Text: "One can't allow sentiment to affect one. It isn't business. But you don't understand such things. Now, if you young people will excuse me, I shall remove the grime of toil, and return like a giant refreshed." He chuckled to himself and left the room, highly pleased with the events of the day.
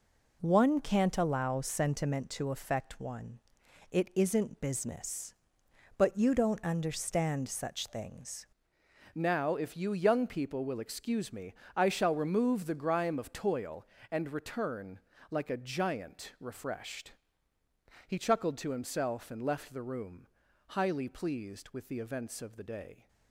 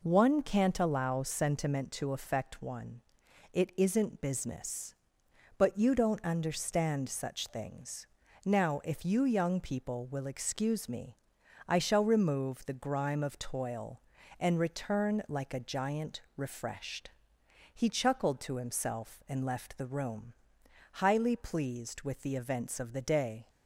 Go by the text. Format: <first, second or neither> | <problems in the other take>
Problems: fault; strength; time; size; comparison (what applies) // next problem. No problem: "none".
second | changes voice at "Now"; from 9.1 s on; 13.9 s long // pauses between "return" and "like"; slight; at 14.9 s; 0.30 s long